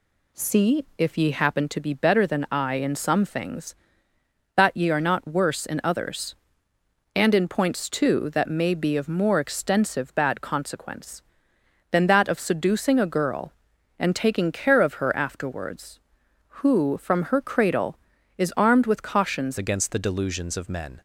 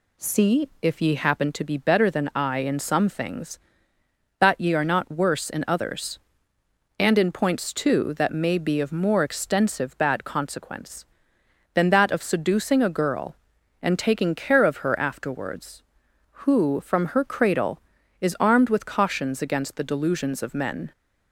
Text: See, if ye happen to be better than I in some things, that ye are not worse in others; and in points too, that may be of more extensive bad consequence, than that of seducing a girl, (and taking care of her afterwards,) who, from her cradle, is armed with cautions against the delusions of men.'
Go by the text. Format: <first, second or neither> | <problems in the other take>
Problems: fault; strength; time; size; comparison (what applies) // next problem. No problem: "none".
second | changes voice at "against"; from 19.5 s on; 1.5 s long